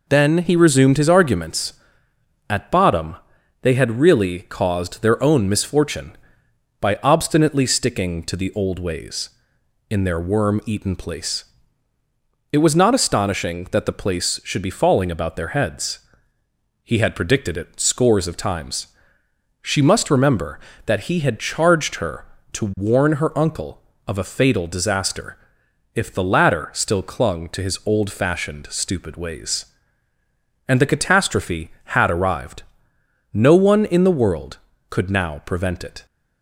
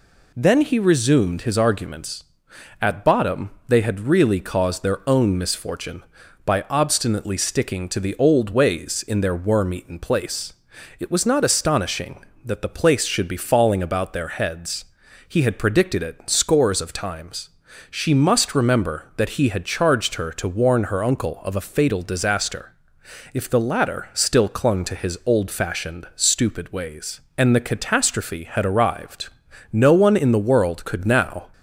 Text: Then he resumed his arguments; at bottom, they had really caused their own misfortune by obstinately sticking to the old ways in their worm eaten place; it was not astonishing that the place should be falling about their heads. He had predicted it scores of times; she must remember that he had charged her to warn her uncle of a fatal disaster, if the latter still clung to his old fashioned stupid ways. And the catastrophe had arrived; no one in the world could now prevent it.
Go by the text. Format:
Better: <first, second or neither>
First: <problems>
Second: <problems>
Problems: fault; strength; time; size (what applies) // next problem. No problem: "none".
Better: first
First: none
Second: stops before "prevent it"; at 31.5 s